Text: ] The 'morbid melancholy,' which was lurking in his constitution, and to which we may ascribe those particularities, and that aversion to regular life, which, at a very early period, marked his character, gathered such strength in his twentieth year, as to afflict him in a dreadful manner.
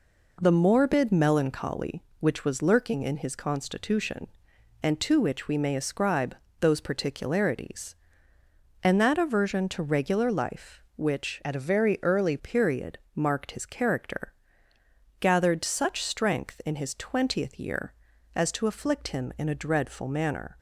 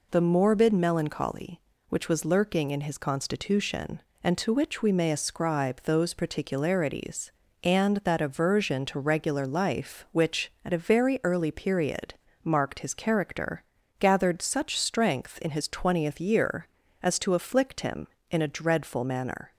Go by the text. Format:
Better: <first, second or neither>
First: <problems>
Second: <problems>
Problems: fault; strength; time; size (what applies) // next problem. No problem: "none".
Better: second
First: pauses between "ascribe" and "those"; slight; at 6.3 s; 0.24 s long // changes voice from "at" to "early"; from 11.4 to 12.3 s; 0.9 s long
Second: none